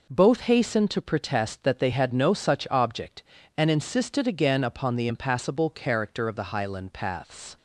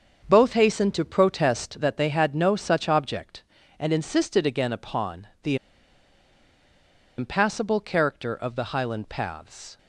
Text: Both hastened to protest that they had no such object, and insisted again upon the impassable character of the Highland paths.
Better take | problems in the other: first | starts louder than the rest; until 1.3 s; 7 dB // pauses between "upon" and "the"; slight; at 5.2 s; 0.16 s long // pauses between "the" and "impassable"; strong; at 5.5 s; 1.6 s long

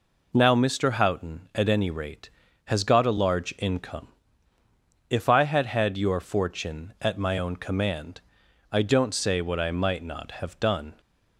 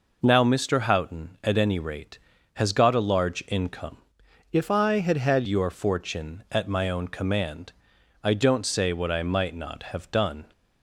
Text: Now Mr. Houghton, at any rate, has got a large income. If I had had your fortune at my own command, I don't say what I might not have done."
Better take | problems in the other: first | changes voice from "If" to "had"; from 4.5 to 5.4 s; 0.9 s long

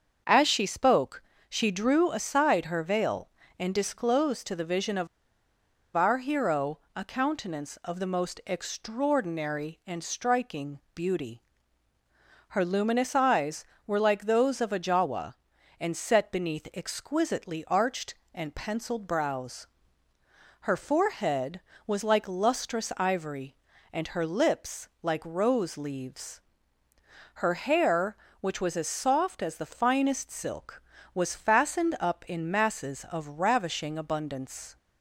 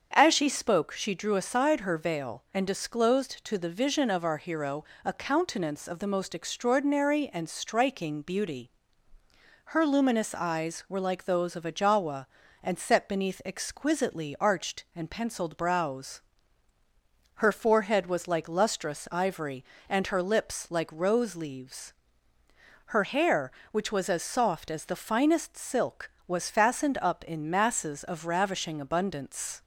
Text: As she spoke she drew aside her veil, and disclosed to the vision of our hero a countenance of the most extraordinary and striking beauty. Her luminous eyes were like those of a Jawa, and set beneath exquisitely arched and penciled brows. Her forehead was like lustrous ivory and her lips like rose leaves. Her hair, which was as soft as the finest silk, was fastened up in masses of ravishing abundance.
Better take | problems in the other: second | starts louder than the rest; until 1.5 s; 7 dB; also in the second // pauses between "spoke" and "she"; slight; at 1.2 s; 0.26 s long // pauses between "of" and "our"; noticeable; at 5.0 s; 0.89 s long // pauses between "hero" and "a"; slight; at 6.7 s; 0.16 s long; slight in the second // pauses between "striking" and "beauty"; slight; at 10.7 s; 0.16 s long // pauses between "lips" and "like"; slight; at 24.8 s; 0.16 s long

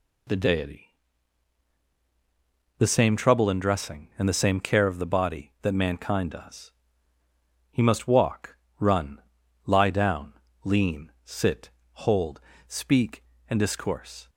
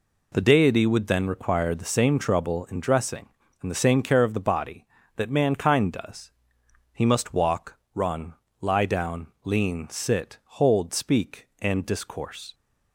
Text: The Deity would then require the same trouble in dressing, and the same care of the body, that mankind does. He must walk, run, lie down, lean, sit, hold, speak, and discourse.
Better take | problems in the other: second | skips "would then require"; at 1.8 s

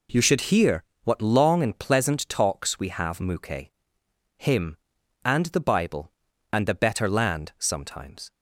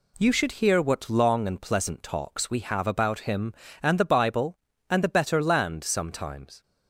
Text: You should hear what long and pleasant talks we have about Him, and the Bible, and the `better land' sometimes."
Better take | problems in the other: second | pauses between "hear" and "what"; slight; at 0.8 s; 0.22 s long // says "muke" for "about"; at 3.1 s

